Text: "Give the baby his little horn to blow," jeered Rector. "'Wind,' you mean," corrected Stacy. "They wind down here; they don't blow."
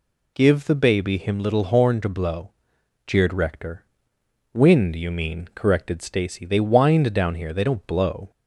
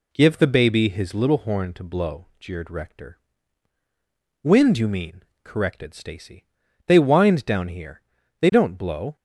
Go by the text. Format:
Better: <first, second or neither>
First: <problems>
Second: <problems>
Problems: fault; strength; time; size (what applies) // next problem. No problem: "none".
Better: second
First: says "him" for "his"; at 1.1 s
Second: none